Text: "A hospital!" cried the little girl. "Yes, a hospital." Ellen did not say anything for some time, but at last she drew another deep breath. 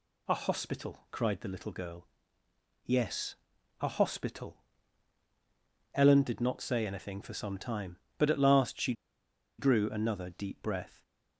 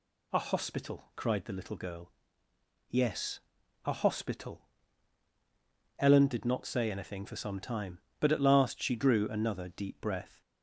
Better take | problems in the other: second | pauses between "she" and "drew"; noticeable; at 8.9 s; 0.65 s long

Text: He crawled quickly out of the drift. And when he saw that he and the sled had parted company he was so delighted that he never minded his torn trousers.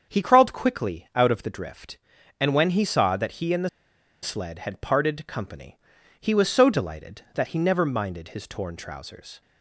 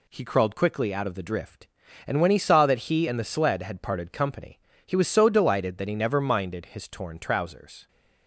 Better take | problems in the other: second | starts louder than the rest; until 1.1 s; 7 dB // pauses between "the" and "sled"; noticeable; at 3.6 s; 0.53 s long // pauses between "company" and "he"; at 5.7 s; 0.44 s long; slight in the second

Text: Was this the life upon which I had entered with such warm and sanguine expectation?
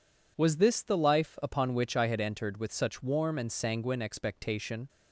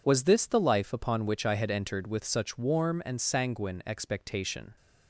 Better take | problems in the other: neither | none

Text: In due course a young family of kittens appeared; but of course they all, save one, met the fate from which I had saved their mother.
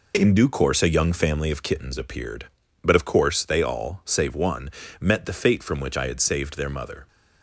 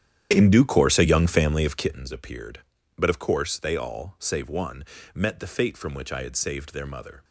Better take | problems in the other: first | starts louder than the rest; strong; until 2.1 s; 10 dB

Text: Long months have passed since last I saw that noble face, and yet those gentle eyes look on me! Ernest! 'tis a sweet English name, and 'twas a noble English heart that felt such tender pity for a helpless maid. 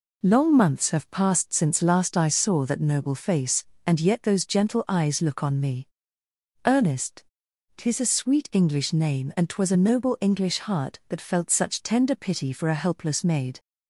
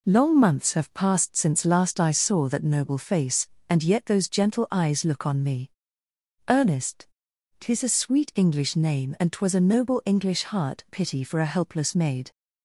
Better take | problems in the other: first | skips "that felt such tender"; at 10.8 s

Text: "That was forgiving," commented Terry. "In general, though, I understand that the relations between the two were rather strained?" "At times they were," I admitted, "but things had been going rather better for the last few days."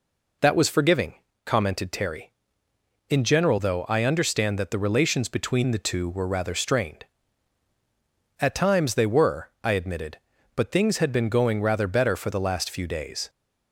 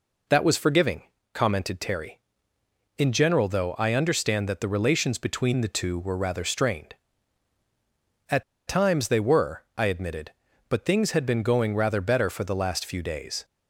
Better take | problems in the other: first | pauses between "At" and "times"; slight; at 8.4 s; 0.25 s long

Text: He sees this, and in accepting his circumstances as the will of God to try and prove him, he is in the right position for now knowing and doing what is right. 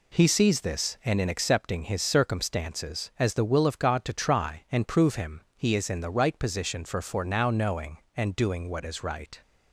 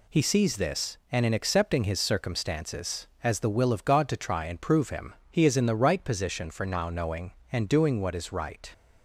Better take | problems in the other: second | says "for" twice; at 7.0 s

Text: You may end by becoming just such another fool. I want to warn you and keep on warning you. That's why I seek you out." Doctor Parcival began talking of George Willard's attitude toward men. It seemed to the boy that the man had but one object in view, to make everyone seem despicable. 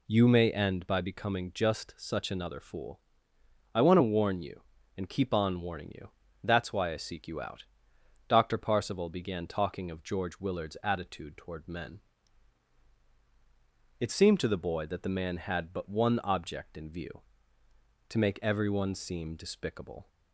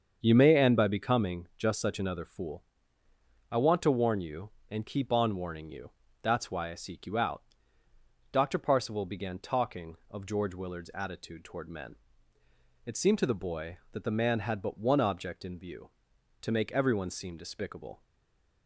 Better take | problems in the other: first | starts louder than the rest; until 1.2 s; 7 dB // stays silent after the last word; slight; from 18.0 s on; 0.6 s long

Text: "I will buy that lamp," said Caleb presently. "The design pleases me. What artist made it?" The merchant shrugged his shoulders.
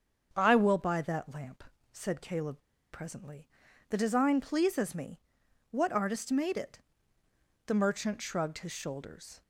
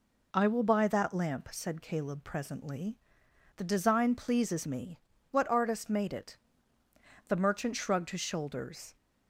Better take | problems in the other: second | starts louder than the rest; until 1.3 s; 7 dB // pauses between "Caleb" and "presently"; slight; at 2.5 s; 0.34 s long

